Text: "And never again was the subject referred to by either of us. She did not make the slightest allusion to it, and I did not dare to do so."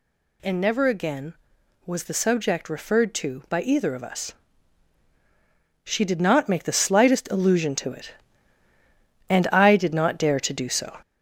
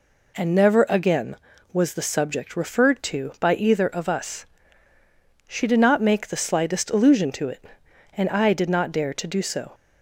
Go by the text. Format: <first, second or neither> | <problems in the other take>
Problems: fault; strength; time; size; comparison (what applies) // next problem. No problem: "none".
second | gets louder; noticeable; throughout; 5 dB